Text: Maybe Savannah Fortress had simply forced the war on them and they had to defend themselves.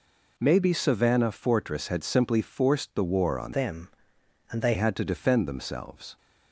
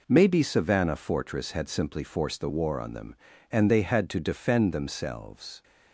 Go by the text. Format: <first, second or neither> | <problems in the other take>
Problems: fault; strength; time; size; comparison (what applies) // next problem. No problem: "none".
second | changes voice from "them" to "they"; from 3.5 to 4.7 s; 1.2 s long